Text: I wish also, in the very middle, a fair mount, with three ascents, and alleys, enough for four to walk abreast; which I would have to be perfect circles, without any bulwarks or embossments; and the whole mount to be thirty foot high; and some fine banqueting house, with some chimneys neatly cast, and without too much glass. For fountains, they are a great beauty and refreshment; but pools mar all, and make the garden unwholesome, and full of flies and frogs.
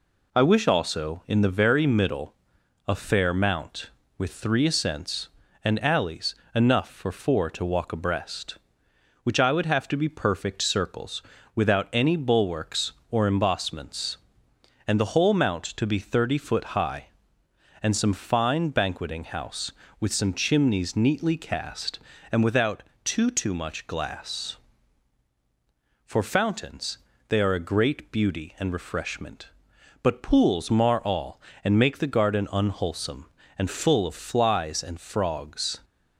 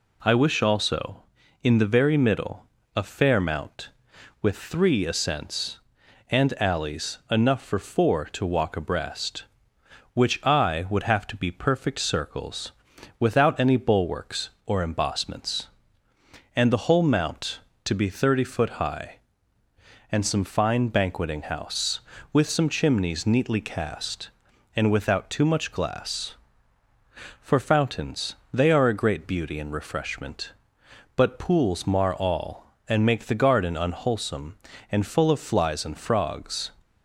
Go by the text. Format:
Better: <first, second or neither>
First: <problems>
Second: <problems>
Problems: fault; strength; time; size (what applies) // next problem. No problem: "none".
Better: second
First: pauses between "without" and "too"; slight; at 22.8 s; 0.18 s long // says "too" twice; at 23.3 s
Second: none